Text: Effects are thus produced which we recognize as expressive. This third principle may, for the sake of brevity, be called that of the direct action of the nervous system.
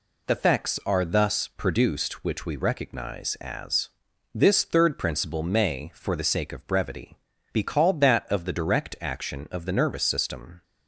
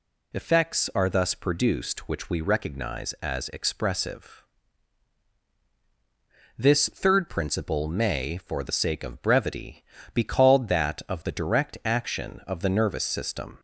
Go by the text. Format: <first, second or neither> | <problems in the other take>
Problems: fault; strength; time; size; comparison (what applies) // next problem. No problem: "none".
second | skips "expressive"; at 4.1 s